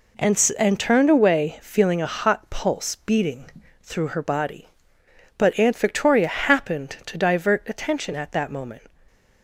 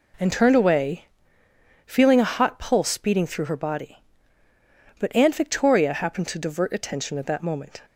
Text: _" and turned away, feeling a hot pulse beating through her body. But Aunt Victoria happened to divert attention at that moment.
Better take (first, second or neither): second